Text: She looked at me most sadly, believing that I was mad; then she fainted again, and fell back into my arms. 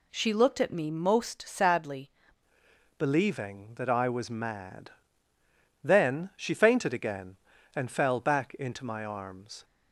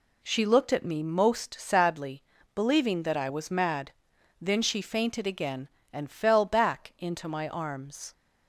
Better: second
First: changes voice at "believing"; from 2.9 s on; 6.7 s long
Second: none

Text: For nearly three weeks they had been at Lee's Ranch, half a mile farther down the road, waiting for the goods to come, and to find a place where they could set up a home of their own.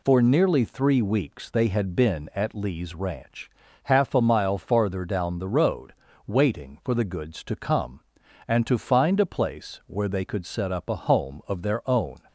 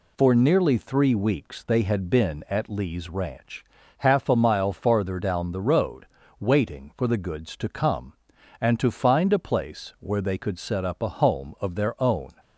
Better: neither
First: none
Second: none

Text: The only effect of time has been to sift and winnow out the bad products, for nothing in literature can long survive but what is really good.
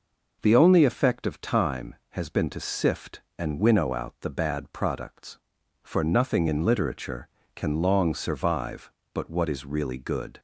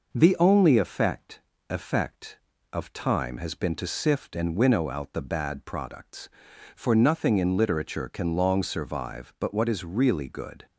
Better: first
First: none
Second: says "effect" twice; at 1.6 s

